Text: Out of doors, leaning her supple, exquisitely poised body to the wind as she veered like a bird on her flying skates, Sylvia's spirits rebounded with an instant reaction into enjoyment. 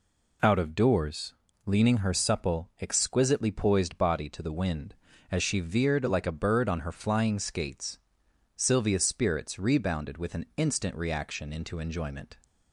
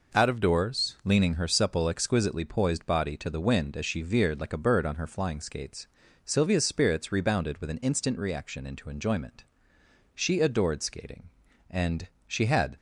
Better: first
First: none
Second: goes on to say "She adored skating and she had"; strong; from 10.1 s on; 2.6 s long

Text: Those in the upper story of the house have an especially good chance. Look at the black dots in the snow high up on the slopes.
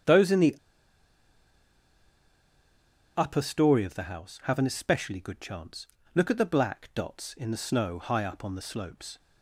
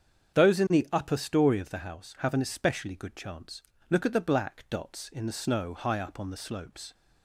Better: second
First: starts louder than the rest; strong; until 3.6 s; 7.5 dB // pauses between "the" and "upper"; strong; at 0.5 s; 2.6 s long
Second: starts louder than the rest; strong; until 1.4 s; 7.5 dB

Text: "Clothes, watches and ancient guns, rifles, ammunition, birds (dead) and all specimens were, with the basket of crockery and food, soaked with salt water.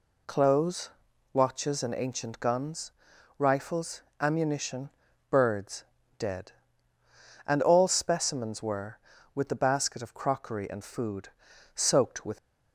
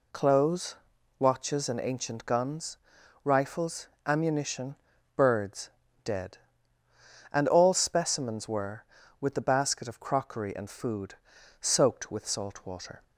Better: second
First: stops before "salt water"; at 12.3 s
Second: none

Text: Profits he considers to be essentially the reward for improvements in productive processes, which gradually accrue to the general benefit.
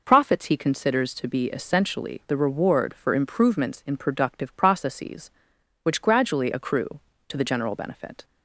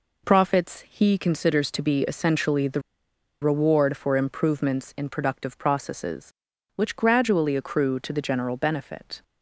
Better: first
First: none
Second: pauses between "the" and "reward"; noticeable; at 2.8 s; 0.61 s long

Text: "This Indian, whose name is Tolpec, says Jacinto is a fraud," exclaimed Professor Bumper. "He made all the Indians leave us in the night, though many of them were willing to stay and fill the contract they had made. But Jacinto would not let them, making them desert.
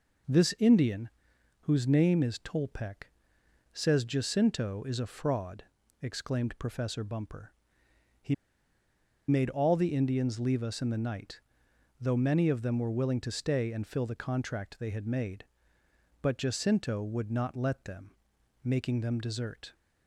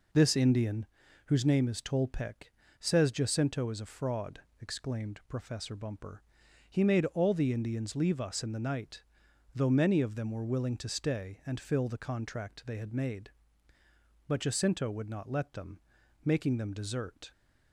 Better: second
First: pauses between "He" and "made"; noticeable; at 8.3 s; 0.93 s long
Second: none

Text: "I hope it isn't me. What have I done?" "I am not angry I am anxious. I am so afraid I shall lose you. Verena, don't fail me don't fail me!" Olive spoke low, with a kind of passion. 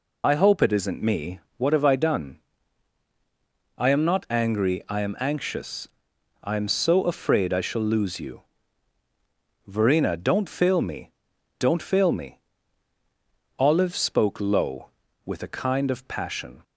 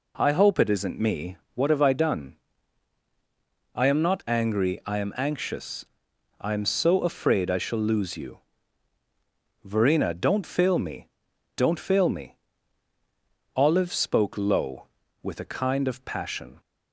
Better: second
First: loses the start of "I"; at 0.2 s; 65 ms // pauses between "me" and "don't"; noticeable; at 11.1 s; 0.48 s long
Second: pauses between "me" and "don't"; noticeable; at 11.0 s; 0.48 s long

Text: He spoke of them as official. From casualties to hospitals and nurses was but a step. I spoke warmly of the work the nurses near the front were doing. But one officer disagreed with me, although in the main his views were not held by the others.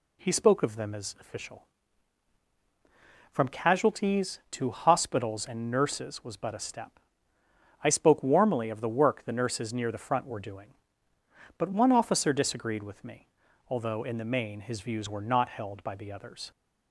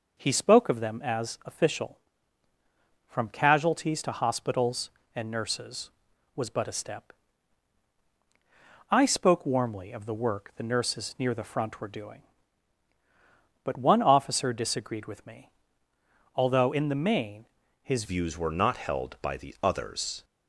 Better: first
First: none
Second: pauses between "main" and "his"; slight; at 17.4 s; 0.36 s long // changes voice at "views"; from 18.0 s on; 2.2 s long

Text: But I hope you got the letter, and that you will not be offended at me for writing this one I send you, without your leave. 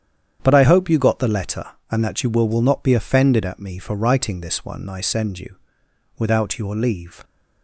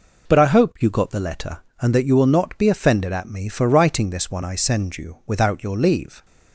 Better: second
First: starts louder than the rest; strong; until 1.4 s; 8.5 dB // says "will" twice; at 2.4 s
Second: none

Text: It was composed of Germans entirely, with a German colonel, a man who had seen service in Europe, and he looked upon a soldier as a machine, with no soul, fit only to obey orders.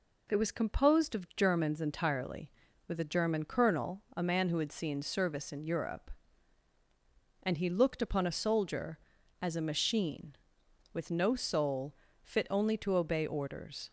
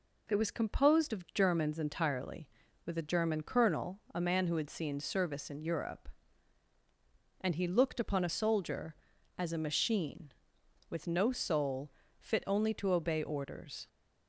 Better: neither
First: none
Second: none

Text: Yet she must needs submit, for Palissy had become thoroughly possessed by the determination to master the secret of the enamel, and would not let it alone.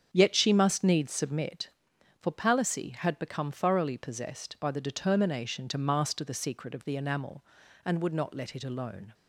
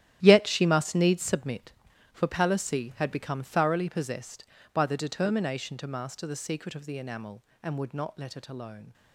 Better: first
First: starts louder than the rest; strong; until 1.1 s; 7.5 dB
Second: gets quieter; strong; throughout; 13.5 dB // starts louder than the rest; strong; until 1.2 s; 11.5 dB

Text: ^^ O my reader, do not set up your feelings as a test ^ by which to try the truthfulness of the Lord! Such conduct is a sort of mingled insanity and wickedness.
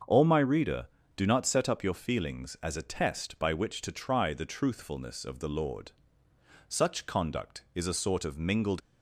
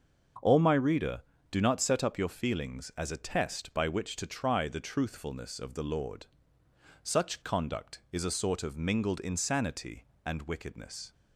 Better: second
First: starts louder than the rest; until 1.3 s; 6.5 dB // stops before "insanity and wickedness"; at 8.8 s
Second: starts louder than the rest; until 1.6 s; 6 dB

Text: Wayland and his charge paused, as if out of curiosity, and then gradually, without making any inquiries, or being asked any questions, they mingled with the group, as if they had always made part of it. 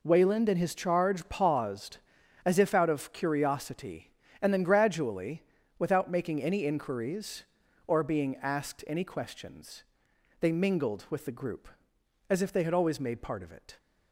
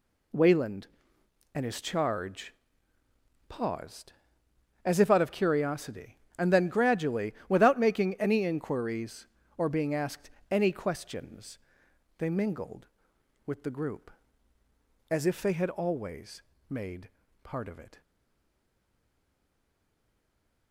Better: first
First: none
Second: pauses between "charge" and "paused"; noticeable; at 2.5 s; 0.96 s long // pauses between "asked" and "any"; slight; at 10.3 s; 0.20 s long // pauses between "always" and "made"; slight; at 16.4 s; 0.26 s long // pauses between "made" and "part"; slight; at 17.0 s; 0.34 s long // stays silent after the last word; strong; from 18.0 s on; 2.7 s long

